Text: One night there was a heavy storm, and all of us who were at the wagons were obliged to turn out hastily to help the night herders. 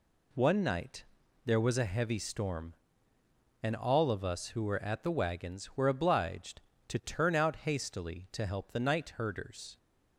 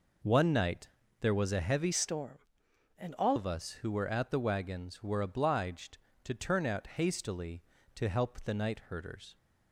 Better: first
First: pauses between "night" and "there"; at 1.0 s; 0.40 s long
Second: pauses between "night" and "there"; slight; at 0.8 s; 0.32 s long // changes voice from "storm" to "all"; from 1.9 to 3.3 s; 1.4 s long

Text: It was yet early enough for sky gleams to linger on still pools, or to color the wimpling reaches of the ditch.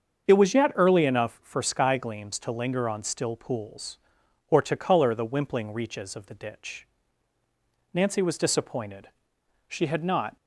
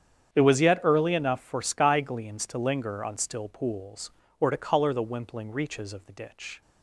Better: second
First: starts louder than the rest; until 1.3 s; 7 dB // goes on to say "Nancy was disappointed she had not"; strong; from 7.9 s on; 2.4 s long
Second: starts louder than the rest; strong; until 1.3 s; 8.5 dB

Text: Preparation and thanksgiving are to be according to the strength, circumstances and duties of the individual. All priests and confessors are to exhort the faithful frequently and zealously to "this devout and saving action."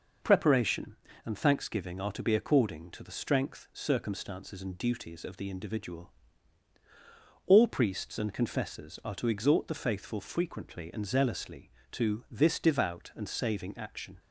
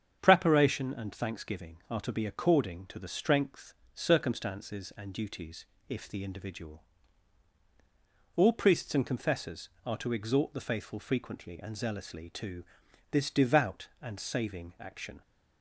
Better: first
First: none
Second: starts louder than the rest; strong; until 1.2 s; 8 dB // says "if" for "of"; at 5.8 s // pauses between "to" and "this"; noticeable; at 12.6 s; 0.48 s long

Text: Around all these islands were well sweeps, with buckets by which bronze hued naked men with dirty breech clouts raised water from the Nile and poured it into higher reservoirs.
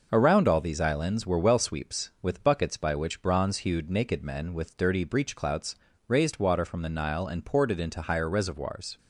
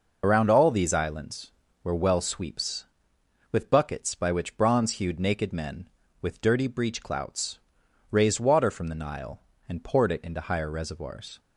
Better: first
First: pauses between "clouts" and "raised"; slight; at 5.7 s; 0.32 s long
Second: loses the start of "Around"; at 0.2 s; 75 ms // pauses between "clouts" and "raised"; noticeable; at 7.5 s; 0.54 s long

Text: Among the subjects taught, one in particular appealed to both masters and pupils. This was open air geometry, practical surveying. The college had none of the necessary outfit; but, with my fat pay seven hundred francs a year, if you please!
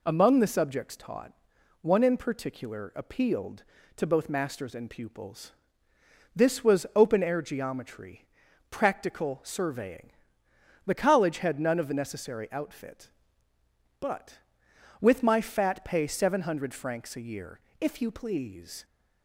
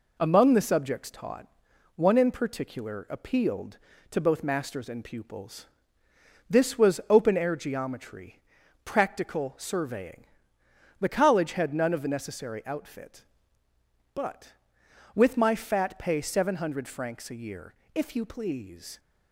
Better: first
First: none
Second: gets quieter; throughout; 3.5 dB

